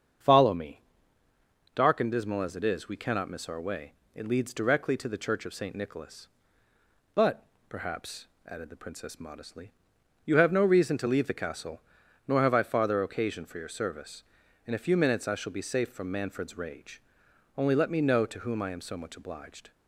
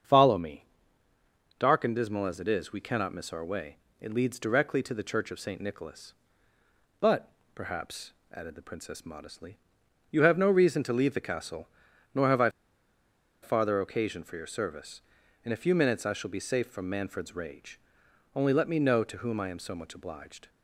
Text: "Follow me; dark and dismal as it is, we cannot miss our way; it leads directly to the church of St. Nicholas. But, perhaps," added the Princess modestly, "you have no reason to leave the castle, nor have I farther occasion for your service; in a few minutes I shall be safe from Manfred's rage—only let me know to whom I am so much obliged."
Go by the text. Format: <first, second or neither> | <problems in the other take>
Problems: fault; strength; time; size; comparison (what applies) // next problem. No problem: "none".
first | starts louder than the rest; until 1.9 s; 7 dB; also in the first // pauses between "I" and "farther"; noticeable; at 12.4 s; 0.93 s long